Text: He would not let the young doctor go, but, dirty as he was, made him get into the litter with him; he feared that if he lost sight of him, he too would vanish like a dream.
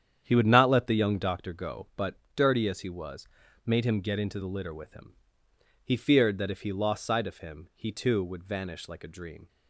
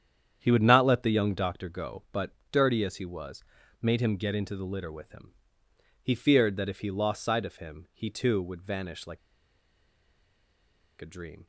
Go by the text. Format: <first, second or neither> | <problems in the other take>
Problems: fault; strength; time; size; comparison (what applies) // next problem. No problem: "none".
first | starts louder than the rest; strong; until 1.4 s; 9 dB; strong in the first // pauses between "like" and "a"; strong; at 9.1 s; 1.8 s long